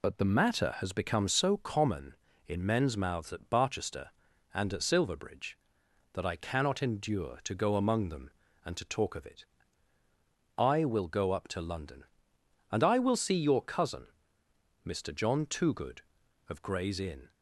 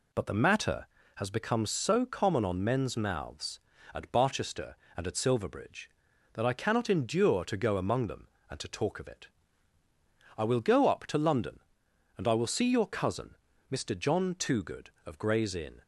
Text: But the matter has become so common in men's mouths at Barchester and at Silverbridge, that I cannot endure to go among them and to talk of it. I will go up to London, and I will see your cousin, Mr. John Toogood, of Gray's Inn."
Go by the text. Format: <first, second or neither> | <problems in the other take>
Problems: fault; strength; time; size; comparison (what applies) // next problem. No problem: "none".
first | says "on" for "in"; at 2.4 s